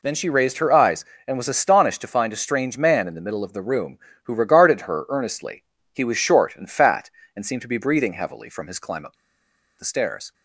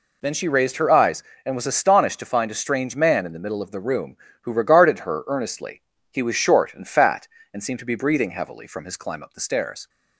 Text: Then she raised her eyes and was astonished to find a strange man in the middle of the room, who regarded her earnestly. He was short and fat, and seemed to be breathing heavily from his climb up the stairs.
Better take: second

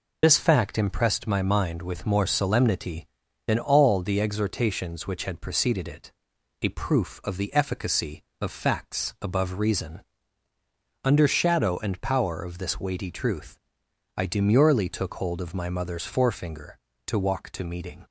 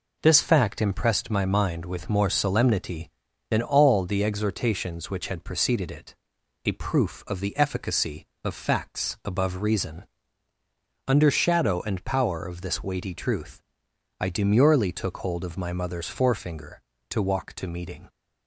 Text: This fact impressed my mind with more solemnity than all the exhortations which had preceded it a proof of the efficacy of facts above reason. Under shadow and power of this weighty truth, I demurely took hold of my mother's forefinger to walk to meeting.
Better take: second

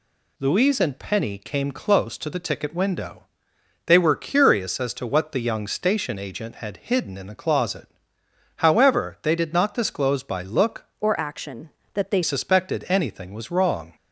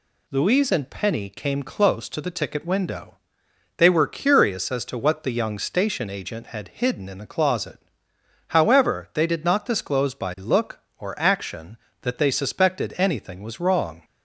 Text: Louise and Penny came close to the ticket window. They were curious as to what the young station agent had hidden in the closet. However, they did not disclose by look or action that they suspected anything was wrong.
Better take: second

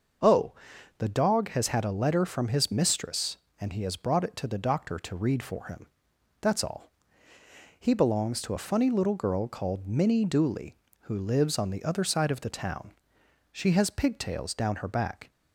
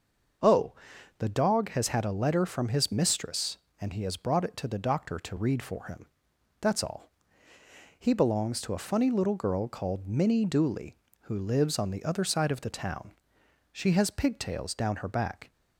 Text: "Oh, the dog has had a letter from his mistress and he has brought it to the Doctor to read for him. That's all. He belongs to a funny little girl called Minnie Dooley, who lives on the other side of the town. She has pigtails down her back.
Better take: neither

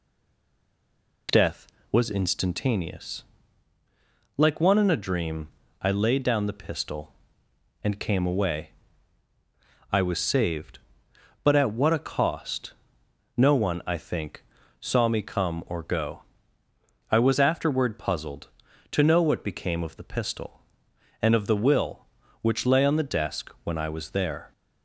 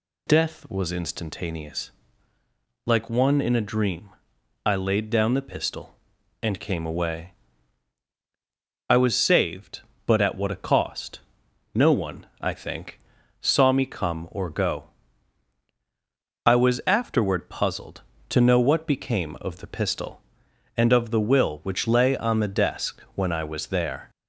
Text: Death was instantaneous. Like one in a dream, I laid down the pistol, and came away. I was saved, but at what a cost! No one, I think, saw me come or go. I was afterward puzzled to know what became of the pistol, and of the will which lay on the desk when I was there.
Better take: second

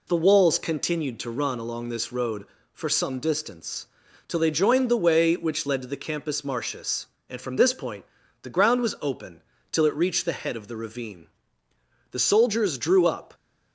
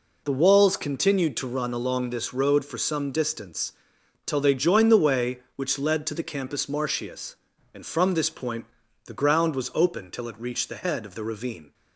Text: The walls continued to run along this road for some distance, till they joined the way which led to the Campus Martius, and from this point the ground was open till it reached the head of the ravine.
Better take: second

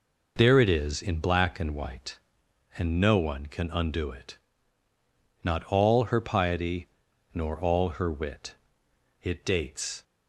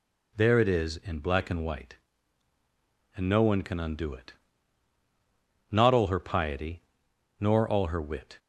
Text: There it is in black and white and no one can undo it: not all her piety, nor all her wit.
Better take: second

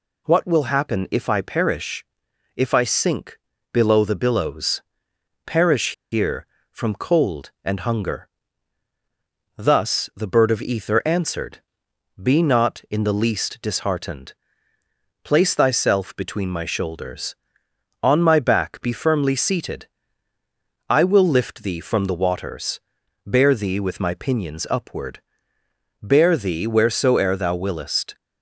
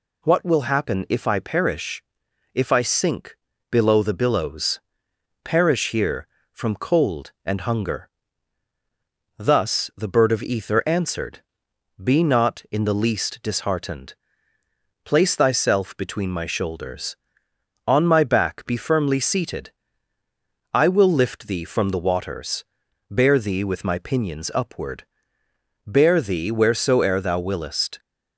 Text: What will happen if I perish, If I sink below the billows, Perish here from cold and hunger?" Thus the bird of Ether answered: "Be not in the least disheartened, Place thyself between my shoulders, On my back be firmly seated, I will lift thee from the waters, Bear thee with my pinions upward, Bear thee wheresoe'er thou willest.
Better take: second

